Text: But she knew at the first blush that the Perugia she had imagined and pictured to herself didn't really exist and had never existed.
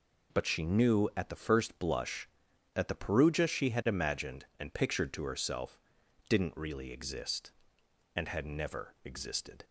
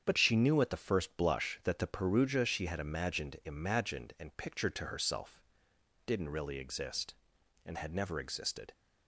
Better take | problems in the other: first | starts louder than the rest; strong; until 1.0 s; 8 dB // says "imagined" twice; at 3.4 s // pauses between "herself" and "didn't"; noticeable; at 5.3 s; 0.66 s long; noticeable in the first

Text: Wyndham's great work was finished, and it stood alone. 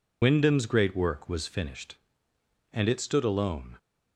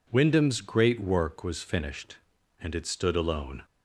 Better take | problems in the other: second | loses the start of "Wyndham's"; at 0.2 s; 45 ms

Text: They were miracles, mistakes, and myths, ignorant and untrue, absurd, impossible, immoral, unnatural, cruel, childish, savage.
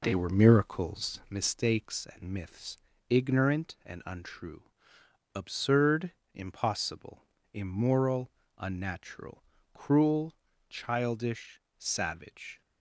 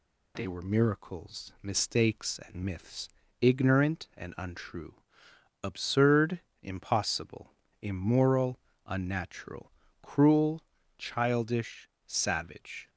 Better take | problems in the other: second | starts louder than the rest; until 1.5 s; 4 dB

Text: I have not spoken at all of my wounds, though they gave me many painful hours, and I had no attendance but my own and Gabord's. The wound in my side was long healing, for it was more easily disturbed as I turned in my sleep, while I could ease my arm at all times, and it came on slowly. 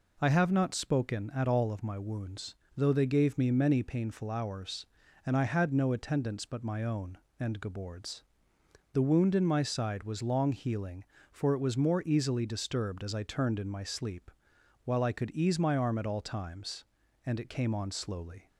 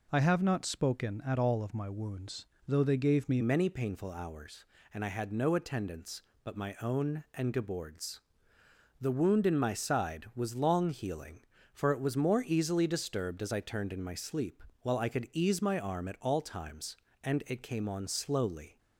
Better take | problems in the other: first | changes voice at "many"; from 3.4 s on; 15.3 s long

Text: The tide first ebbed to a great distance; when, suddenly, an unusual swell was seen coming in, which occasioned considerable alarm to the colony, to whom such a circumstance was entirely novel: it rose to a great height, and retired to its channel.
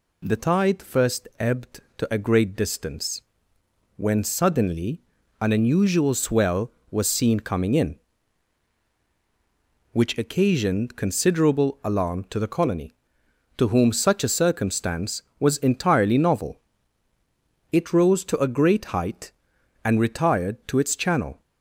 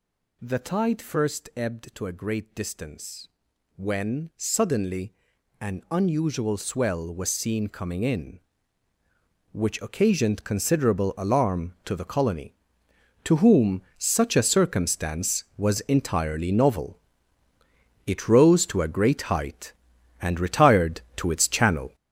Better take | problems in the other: first | gets louder; strong; throughout; 8.5 dB // pauses between "whom" and "such"; slight; at 13.8 s; 0.16 s long

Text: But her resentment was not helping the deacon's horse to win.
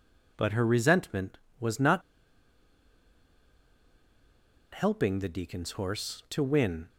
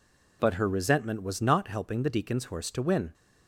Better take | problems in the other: second | pauses between "not" and "helping"; strong; at 2.0 s; 2.7 s long

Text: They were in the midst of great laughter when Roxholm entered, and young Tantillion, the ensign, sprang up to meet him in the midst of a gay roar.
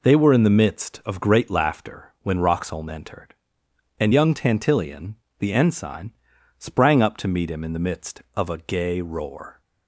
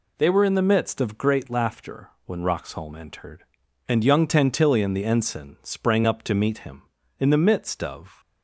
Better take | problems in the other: first | pauses between "laughter" and "when"; slight; at 2.0 s; 0.16 s long // stops before "a gay roar"; at 8.1 s

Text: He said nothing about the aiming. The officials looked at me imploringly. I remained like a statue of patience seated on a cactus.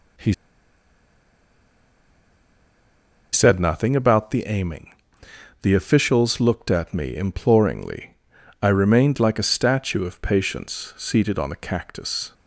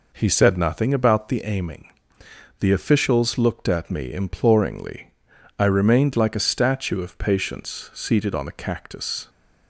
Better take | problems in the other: second | pauses between "He" and "said"; strong; at 0.3 s; 2.9 s long

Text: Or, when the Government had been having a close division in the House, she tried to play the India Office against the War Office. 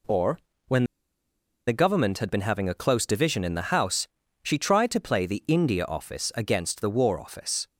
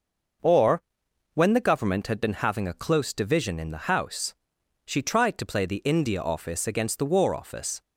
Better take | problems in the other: second | pauses between "when" and "the"; noticeable; at 0.8 s; 0.83 s long

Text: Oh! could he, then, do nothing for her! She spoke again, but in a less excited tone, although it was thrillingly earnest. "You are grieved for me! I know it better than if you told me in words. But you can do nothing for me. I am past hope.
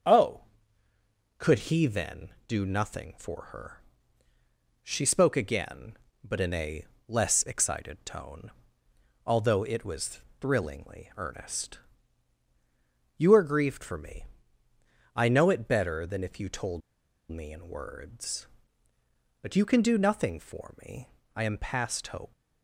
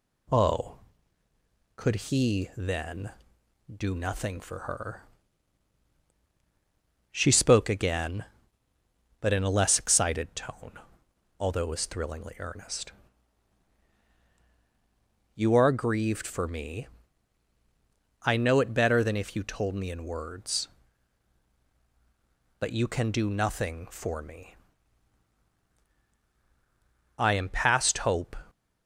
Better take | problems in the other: second | starts louder than the rest; strong; until 2.0 s; 7.5 dB // pauses between "a" and "less"; slight; at 6.8 s; 0.22 s long // pauses between "was" and "thrillingly"; slight; at 10.1 s; 0.20 s long // pauses between "told" and "me"; noticeable; at 16.8 s; 0.49 s long

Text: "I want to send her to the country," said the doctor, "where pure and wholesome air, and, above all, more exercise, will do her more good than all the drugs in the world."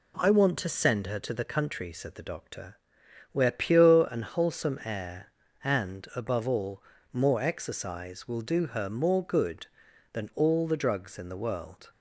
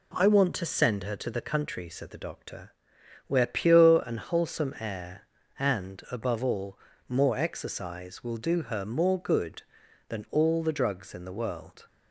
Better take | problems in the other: neither | none

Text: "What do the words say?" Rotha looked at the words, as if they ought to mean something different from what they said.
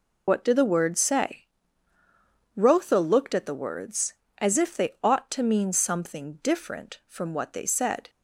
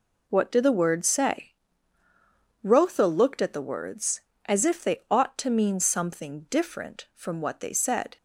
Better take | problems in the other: second | loses the start of "What"; at 0.2 s; 65 ms

